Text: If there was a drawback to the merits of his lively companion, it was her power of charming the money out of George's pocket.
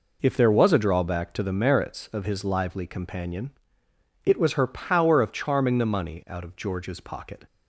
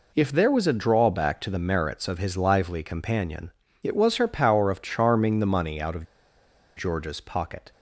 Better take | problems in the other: first | pauses between "of" and "George's"; noticeable; at 6.0 s; 0.71 s long

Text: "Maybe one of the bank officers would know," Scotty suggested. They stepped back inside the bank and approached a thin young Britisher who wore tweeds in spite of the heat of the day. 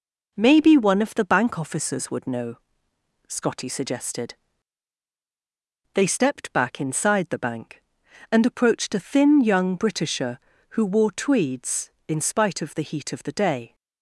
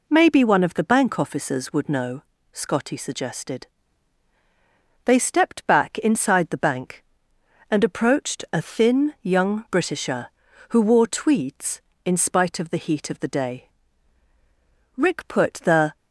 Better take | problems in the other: first | goes on to say "Rick put the"; noticeable; from 14.9 s on; 1.0 s long

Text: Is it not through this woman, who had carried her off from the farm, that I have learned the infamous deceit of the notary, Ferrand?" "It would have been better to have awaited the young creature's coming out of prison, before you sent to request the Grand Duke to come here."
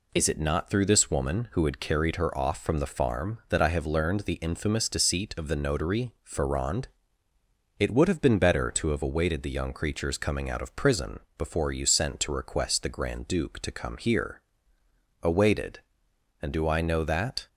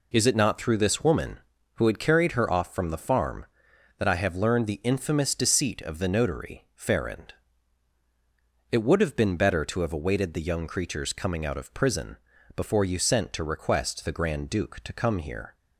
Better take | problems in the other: second | goes on to say "Awaited And do I know that"; strong; from 15.2 s on; 2.2 s long

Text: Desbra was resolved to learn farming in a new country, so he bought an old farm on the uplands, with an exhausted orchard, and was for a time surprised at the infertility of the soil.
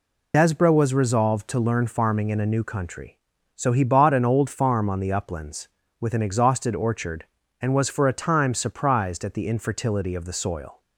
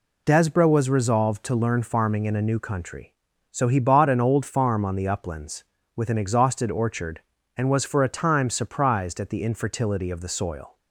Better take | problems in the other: second | loses the start of "Desbra"; at 0.3 s; 55 ms

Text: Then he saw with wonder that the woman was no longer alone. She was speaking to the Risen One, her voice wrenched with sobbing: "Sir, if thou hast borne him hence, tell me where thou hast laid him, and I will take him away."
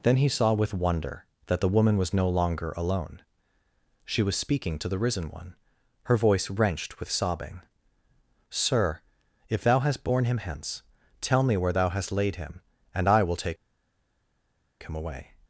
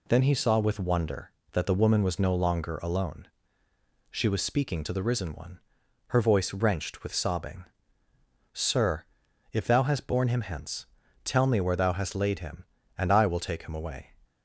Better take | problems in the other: second | pauses between "take" and "him"; strong; at 13.5 s; 1.2 s long

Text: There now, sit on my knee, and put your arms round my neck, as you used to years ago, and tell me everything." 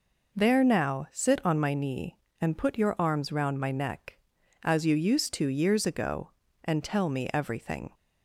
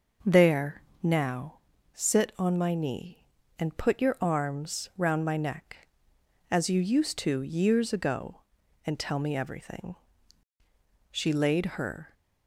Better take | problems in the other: first | pauses between "There" and "now"; slight; at 0.8 s; 0.18 s long // goes on to say "She laid her"; noticeable; from 11.1 s on; 1.0 s long

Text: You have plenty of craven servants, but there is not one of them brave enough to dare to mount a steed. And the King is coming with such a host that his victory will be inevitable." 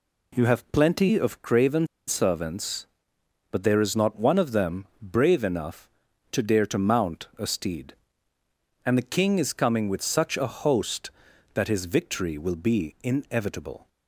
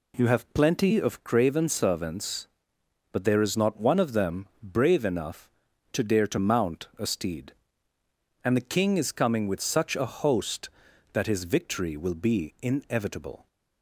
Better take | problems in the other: second | pauses between "craven" and "servants"; slight; at 1.8 s; 0.22 s long // pauses between "them" and "brave"; slight; at 4.8 s; 0.16 s long; slight in the second

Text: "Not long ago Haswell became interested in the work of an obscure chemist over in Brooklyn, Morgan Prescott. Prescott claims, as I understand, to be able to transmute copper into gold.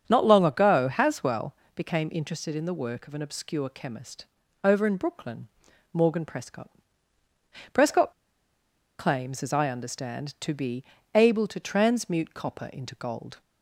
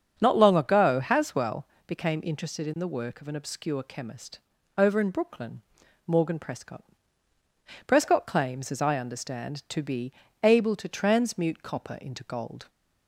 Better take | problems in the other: second | starts louder than the rest; until 1.0 s; 7 dB; also in the second // pauses between "Haswell" and "became"; slight; at 1.5 s; 0.20 s long; slight in the second // pauses between "chemist" and "over"; at 4.2 s; 0.38 s long; also in the second // pauses between "Prescott" and "claims"; noticeable; at 8.1 s; 0.85 s long // pauses between "be" and "able"; slight; at 10.8 s; 0.32 s long; slight in the second

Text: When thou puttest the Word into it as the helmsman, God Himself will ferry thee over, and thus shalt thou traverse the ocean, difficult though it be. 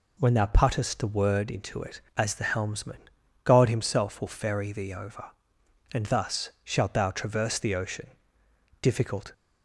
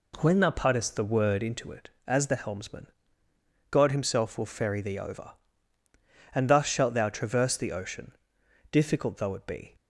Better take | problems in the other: second | stops before "though it be"; at 9.3 s

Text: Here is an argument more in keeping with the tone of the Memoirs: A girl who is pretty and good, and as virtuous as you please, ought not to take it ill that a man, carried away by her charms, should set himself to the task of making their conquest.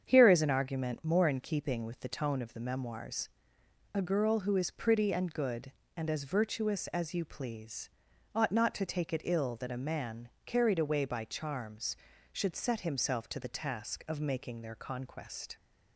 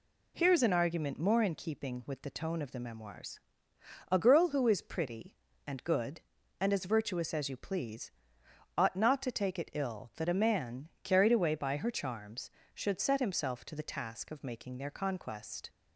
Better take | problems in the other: second | starts louder than the rest; strong; until 1.0 s; 7.5 dB // skips "her"; at 11.2 s

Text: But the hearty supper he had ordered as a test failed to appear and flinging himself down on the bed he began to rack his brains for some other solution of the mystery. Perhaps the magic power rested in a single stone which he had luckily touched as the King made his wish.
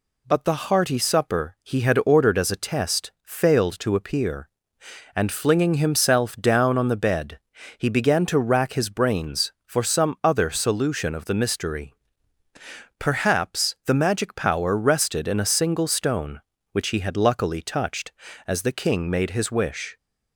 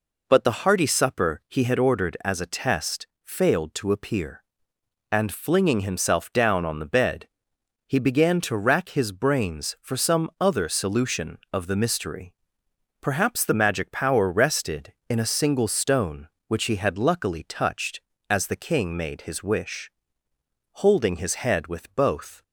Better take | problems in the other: first | pauses between "test" and "failed"; slight; at 3.0 s; 0.16 s long // pauses between "bed" and "he"; noticeable; at 7.2 s; 0.60 s long; also in the first // goes on to say "Holding his head with both"; strong; from 20.7 s on; 1.7 s long

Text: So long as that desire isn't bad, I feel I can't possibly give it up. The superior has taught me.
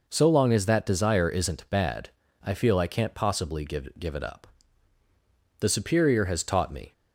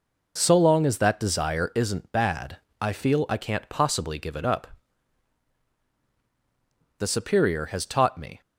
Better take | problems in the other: second | says "give" twice; at 3.9 s

